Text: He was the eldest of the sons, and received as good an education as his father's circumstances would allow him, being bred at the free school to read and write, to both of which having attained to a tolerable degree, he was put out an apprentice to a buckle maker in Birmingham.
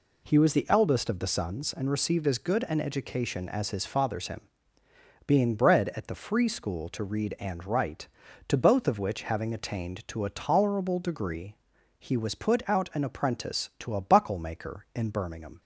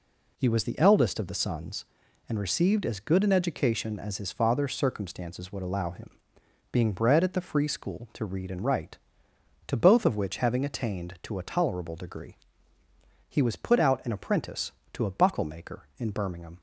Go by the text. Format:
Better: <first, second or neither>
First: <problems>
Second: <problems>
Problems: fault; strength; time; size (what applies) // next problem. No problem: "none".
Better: second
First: skips "circumstances would allow"; at 4.2 s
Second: none